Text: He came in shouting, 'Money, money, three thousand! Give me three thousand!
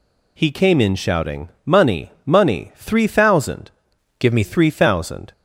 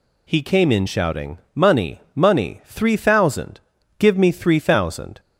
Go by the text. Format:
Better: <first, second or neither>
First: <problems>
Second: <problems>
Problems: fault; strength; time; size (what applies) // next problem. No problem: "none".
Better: second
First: changes voice from "Give" to "me"; from 4.1 to 4.4 s; 0.3 s long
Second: none